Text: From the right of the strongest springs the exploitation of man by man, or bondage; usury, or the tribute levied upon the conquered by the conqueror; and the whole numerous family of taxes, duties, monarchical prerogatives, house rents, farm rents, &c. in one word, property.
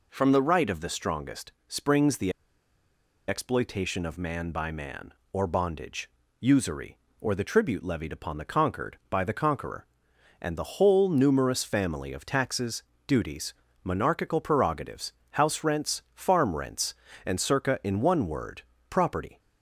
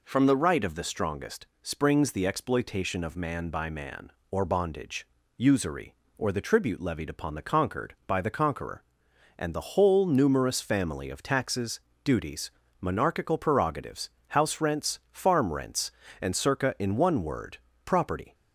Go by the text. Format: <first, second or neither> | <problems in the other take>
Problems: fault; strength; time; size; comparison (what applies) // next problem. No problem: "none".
second | pauses between "strongest" and "springs"; slight; at 1.5 s; 0.16 s long; slight in the second // pauses between "the" and "exploitation"; noticeable; at 2.3 s; 0.96 s long